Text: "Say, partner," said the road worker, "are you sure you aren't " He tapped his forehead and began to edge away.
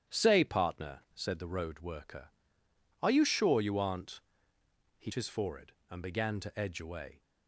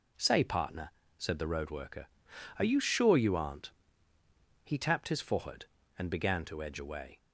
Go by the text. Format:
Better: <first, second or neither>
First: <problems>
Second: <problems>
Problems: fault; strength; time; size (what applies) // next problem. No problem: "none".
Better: second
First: starts louder than the rest; strong; until 1.2 s; 11 dB // skips "tapped"; at 5.1 s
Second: none